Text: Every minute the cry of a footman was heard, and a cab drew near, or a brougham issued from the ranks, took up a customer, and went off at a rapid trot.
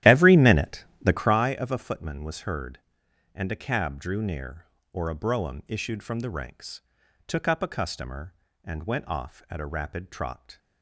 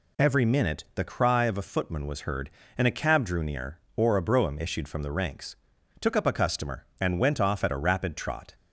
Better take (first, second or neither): second